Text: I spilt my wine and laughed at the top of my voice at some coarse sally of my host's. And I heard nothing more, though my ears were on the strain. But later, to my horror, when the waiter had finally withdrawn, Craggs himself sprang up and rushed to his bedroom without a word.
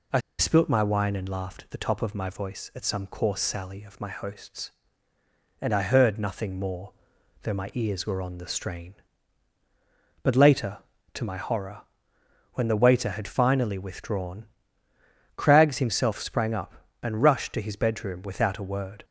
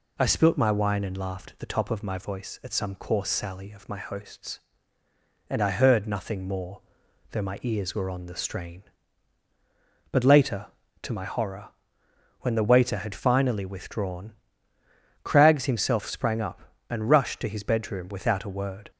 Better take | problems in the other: second | pauses between "I" and "spilt"; slight; at 0.1 s; 0.20 s long

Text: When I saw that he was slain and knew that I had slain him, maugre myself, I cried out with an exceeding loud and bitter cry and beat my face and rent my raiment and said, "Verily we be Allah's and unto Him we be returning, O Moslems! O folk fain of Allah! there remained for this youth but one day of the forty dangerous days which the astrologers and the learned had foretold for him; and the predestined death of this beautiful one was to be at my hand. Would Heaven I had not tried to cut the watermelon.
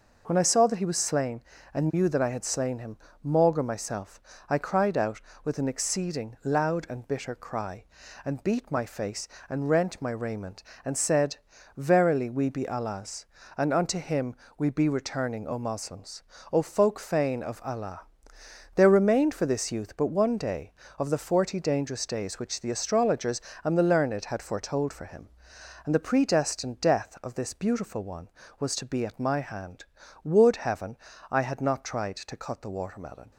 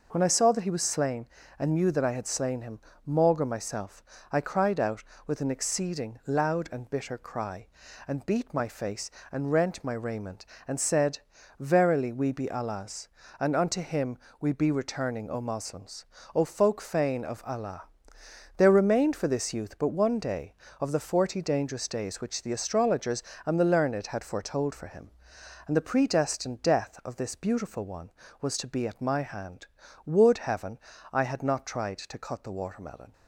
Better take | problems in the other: neither | pauses between "Him" and "we"; slight; the same in both // pauses between "Heaven" and "I"; slight; the same in both

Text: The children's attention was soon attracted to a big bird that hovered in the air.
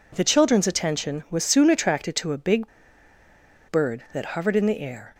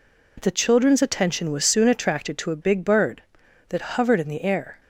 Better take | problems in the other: second | pauses between "big" and "bird"; at 2.6 s; 1.0 s long

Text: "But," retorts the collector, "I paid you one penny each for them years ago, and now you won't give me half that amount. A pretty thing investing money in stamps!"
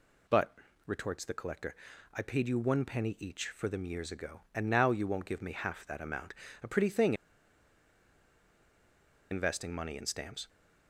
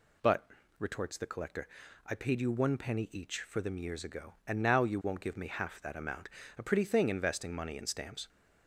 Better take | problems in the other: second | pauses between "thing" and "investing"; strong; at 7.1 s; 2.1 s long

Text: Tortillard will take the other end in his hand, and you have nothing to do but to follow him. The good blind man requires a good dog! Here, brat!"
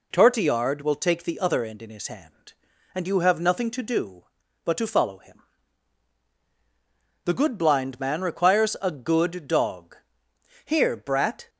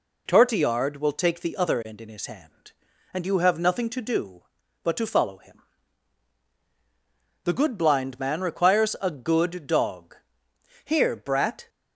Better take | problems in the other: neither | none

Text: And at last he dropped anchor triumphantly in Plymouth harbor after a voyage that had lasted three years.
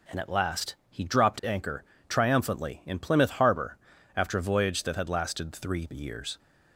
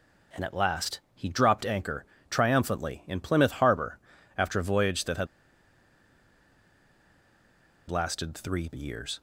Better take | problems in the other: first | pauses between "anchor" and "triumphantly"; slight; at 2.0 s; 0.24 s long; slight in the first // pauses between "harbor" and "after"; at 3.9 s; 0.40 s long; also in the first // pauses between "had" and "lasted"; strong; at 5.2 s; 2.6 s long

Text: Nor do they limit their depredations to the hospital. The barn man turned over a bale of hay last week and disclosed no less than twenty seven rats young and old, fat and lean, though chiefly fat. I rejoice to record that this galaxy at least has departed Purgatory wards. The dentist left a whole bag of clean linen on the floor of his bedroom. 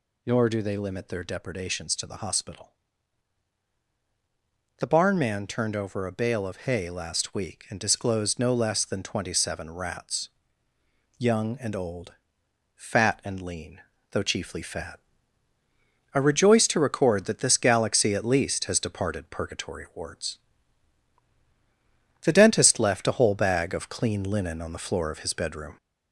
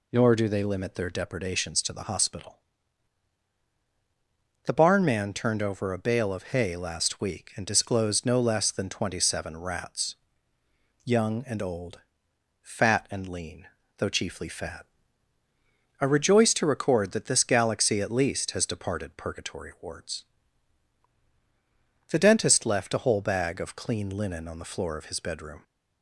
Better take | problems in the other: second | gets louder; throughout; 3.5 dB // pauses between "rats" and "young"; noticeable; at 10.2 s; 0.90 s long; noticeable in the second

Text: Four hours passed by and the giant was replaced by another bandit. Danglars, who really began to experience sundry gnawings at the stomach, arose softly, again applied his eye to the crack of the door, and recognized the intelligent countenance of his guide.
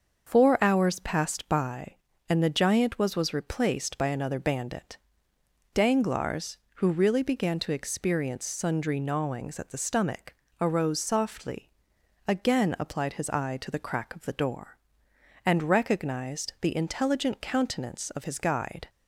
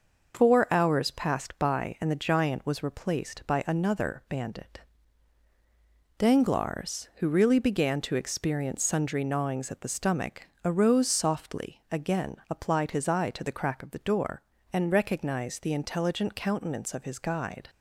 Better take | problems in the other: second | starts louder than the rest; until 1.3 s; 6.5 dB // says "was" twice; at 3.1 s

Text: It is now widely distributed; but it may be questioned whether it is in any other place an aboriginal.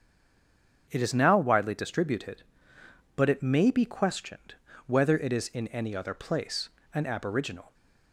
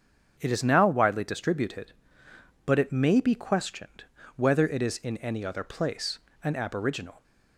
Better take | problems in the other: second | stays silent before the first word; slight; until 0.8 s; 0.8 s long // starts louder than the rest; strong; until 1.9 s; 7 dB; strong in the second // pauses between "questioned" and "whether"; slight; at 4.5 s; 0.32 s long; slight in the second // pauses between "place" and "an"; slight; at 6.6 s; 0.24 s long; slight in the second

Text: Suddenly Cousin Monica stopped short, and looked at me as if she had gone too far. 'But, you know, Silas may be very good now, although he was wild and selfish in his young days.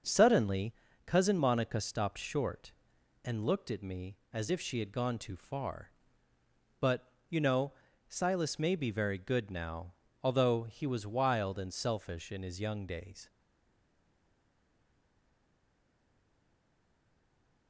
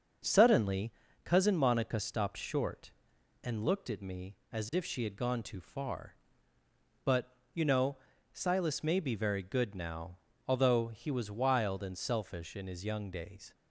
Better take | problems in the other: second | starts louder than the rest; until 1.3 s; 6.5 dB; also in the second // pauses between "Suddenly" and "Cousin"; slight; at 0.7 s; 0.32 s long; slight in the second // stays silent after the last word; strong; from 13.2 s on; 4.4 s long

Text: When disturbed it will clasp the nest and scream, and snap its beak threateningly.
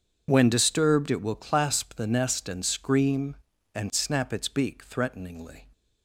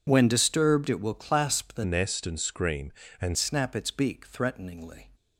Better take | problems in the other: first | changes voice from "nest" to "and"; from 1.8 to 3.3 s; 1.5 s long

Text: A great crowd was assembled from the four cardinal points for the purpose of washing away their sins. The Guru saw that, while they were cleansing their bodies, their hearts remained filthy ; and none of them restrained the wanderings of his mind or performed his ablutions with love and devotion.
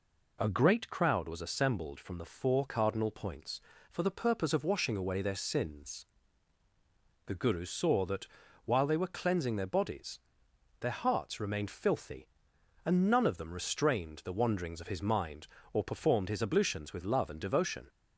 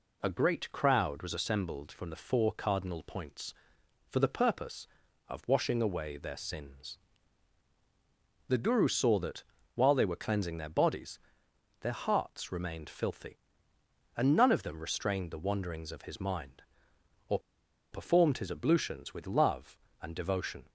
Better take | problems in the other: first | pauses between "or" and "performed"; noticeable; at 17.3 s; 0.53 s long

